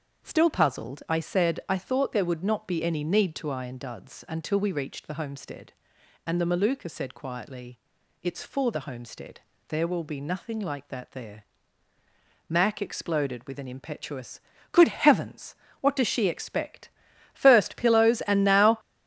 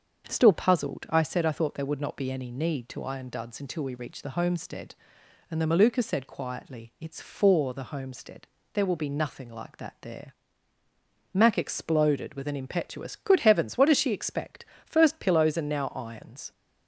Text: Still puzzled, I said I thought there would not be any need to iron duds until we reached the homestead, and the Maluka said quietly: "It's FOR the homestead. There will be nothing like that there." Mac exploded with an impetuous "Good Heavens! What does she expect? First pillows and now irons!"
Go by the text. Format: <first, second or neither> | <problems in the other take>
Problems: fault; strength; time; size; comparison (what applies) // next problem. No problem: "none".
second | starts louder than the rest; until 1.3 s; 7 dB; also in the second // pauses between "impetuous" and "Good"; slight; at 14.3 s; 0.32 s long // stops before "irons"; at 18.7 s